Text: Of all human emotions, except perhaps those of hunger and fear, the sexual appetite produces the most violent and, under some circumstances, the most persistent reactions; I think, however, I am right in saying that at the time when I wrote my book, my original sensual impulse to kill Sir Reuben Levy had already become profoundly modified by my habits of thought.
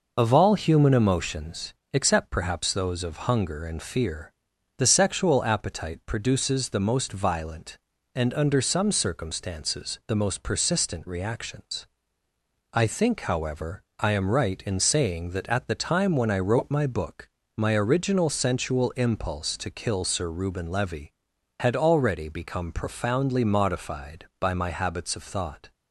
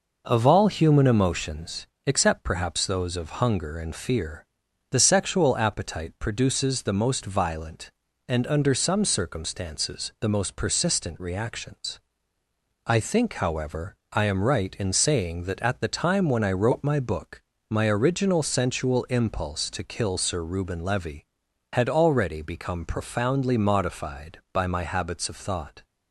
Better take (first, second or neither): second